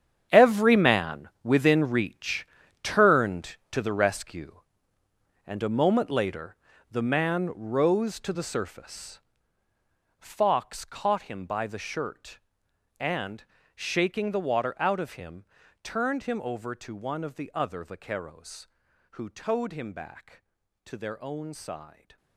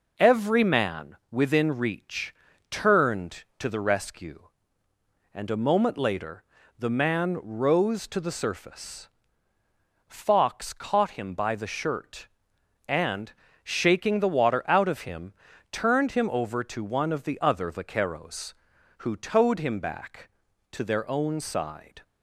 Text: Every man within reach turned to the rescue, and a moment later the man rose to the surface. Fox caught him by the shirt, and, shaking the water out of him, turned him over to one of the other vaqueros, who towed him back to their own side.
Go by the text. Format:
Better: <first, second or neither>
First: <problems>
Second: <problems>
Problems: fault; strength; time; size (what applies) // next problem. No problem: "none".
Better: second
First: gets quieter; strong; throughout; 14 dB // pauses between "reach" and "turned"; at 2.4 s; 0.38 s long // pauses between "later" and "the"; slight; at 6.5 s; 0.34 s long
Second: pauses between "reach" and "turned"; at 2.3 s; 0.38 s long // pauses between "later" and "the"; slight; at 6.4 s; 0.34 s long